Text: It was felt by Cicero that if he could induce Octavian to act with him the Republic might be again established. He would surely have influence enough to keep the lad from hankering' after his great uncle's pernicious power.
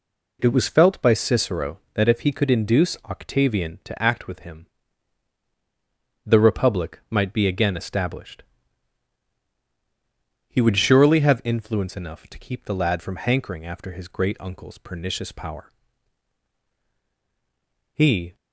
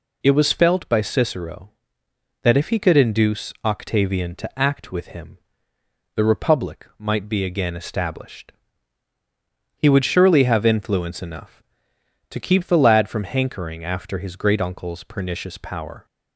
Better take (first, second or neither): second